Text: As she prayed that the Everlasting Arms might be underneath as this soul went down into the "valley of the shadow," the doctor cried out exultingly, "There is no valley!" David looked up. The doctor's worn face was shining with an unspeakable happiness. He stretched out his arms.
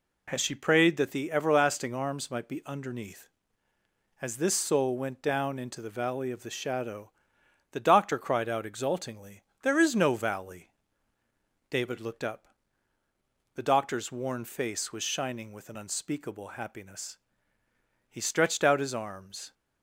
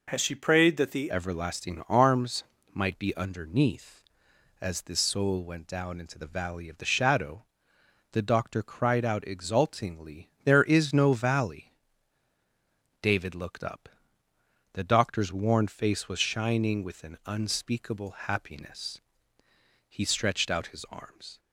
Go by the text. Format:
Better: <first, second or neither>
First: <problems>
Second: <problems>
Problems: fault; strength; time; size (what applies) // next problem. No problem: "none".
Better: first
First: none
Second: changes voice at "Everlasting"; from 1.1 s on; 20.2 s long // pauses between "Arms" and "might"; slight; at 2.4 s; 0.30 s long